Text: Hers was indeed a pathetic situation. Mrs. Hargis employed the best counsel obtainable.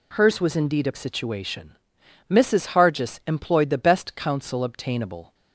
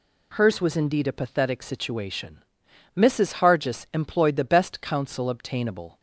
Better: second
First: skips "pathetic"; at 0.9 s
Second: none

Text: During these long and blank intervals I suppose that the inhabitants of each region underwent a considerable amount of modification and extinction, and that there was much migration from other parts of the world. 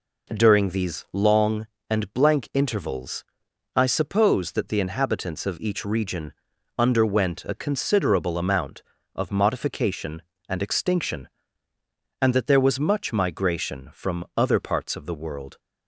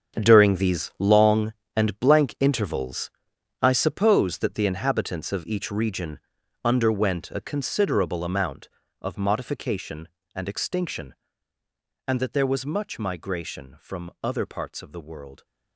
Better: first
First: pauses between "intervals" and "I"; noticeable; at 3.2 s; 0.50 s long // pauses between "region" and "underwent"; at 6.3 s; 0.44 s long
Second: gets quieter; strong; throughout; 12 dB // pauses between "intervals" and "I"; noticeable; at 3.1 s; 0.50 s long // pauses between "region" and "underwent"; at 6.1 s; 0.44 s long

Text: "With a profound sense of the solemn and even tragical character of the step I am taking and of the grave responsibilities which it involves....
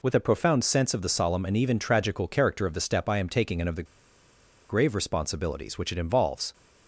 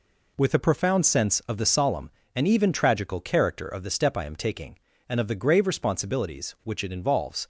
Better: second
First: pauses between "the" and "grave"; noticeable; at 3.8 s; 0.83 s long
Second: none

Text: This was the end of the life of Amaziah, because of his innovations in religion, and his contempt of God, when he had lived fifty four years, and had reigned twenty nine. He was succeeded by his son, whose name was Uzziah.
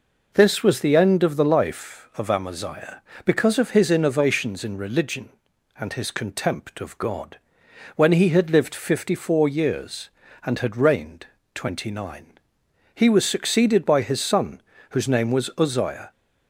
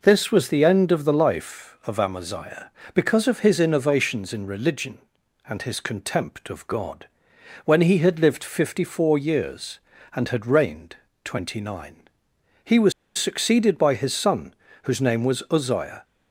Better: first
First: pauses between "reigned" and "twenty"; slight; at 11.2 s; 0.30 s long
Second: pauses between "reigned" and "twenty"; slight; at 10.9 s; 0.30 s long // pauses between "was" and "succeeded"; slight; at 12.9 s; 0.25 s long

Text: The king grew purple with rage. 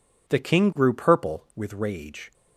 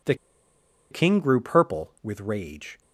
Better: first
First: none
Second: pauses between "The" and "king"; noticeable; at 0.1 s; 0.76 s long

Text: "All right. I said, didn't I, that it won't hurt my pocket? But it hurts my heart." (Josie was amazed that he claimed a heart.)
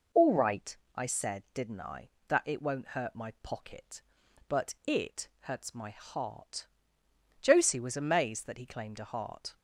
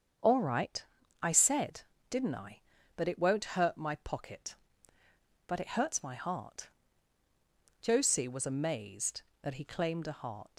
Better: first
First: none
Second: starts louder than the rest; strong; until 1.6 s; 7.5 dB // leaves "heart" unfinished; at 10.5 s; 95 ms

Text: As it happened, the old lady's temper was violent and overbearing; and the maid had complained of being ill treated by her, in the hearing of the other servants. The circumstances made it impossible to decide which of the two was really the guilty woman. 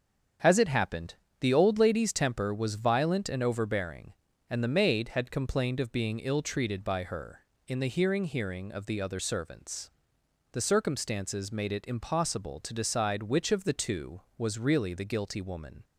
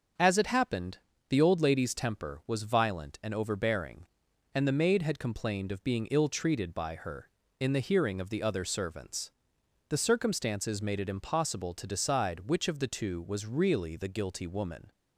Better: second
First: starts louder than the rest; strong; until 1.6 s; 7.5 dB // says "hearing" twice; at 8.2 s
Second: starts louder than the rest; until 1.4 s; 6.5 dB

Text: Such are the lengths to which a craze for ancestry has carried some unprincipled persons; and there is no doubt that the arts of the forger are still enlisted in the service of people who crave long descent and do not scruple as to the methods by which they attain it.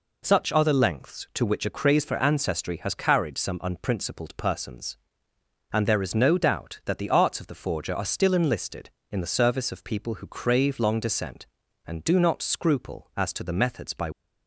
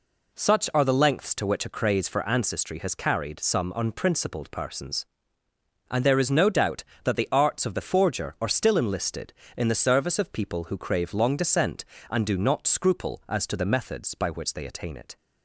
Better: second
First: stops before "which they attain it"; at 14.1 s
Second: none

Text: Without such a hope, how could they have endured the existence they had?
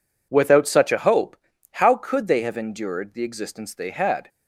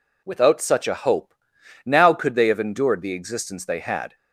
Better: first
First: none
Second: says "now" for "how"; at 1.8 s

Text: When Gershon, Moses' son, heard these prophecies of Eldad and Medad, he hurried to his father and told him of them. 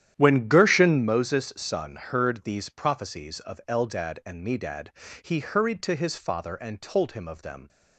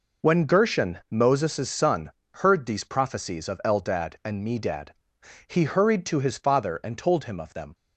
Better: second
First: starts louder than the rest; strong; until 1.1 s; 10.5 dB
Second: none

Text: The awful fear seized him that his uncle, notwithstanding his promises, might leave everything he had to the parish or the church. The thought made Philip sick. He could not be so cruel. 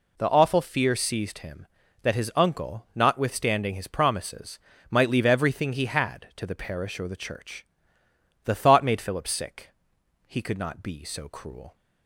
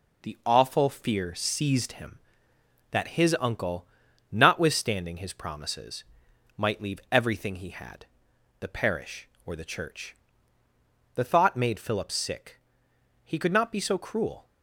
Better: first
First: none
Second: skips "to"; at 8.3 s

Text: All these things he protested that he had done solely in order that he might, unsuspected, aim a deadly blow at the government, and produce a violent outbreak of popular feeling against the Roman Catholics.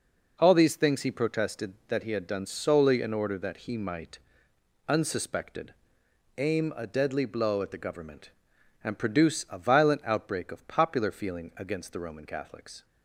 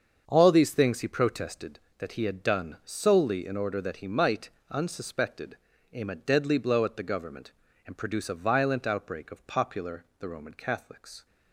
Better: first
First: none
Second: starts louder than the rest; until 1.2 s; 7 dB // skips "feeling against"; at 10.1 s

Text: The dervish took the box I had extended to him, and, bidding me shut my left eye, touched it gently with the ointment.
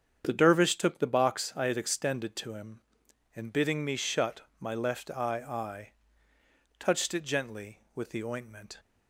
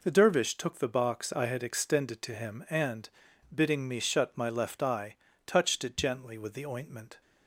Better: second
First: starts louder than the rest; strong; until 1.2 s; 8 dB // pauses between "shut" and "my"; slight; at 4.4 s; 0.18 s long // says "eye" twice; at 5.4 s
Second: none

